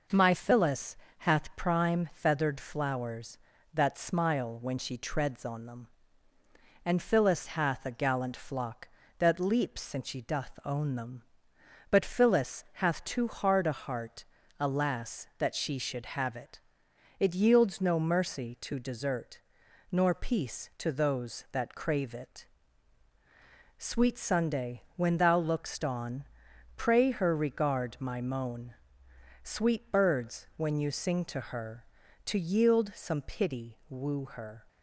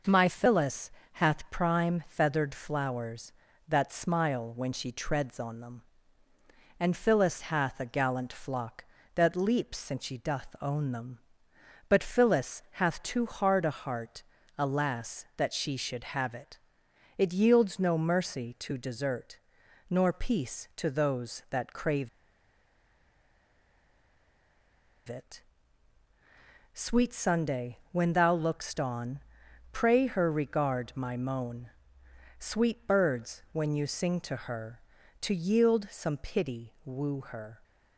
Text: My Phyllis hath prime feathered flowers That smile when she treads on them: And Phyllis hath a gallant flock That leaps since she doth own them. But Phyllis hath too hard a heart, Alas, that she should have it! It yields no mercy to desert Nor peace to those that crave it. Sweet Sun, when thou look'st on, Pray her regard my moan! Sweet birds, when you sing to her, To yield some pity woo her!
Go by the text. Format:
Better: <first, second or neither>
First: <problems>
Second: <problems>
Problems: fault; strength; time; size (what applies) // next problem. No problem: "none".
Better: first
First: pauses between "Phyllis" and "hath"; slight; at 0.9 s; 0.24 s long // pauses between "desert" and "Nor"; noticeable; at 19.3 s; 0.50 s long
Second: pauses between "Phyllis" and "hath"; slight; at 0.8 s; 0.24 s long // pauses between "desert" and "Nor"; noticeable; at 19.3 s; 0.50 s long // pauses between "crave" and "it"; strong; at 22.0 s; 3.0 s long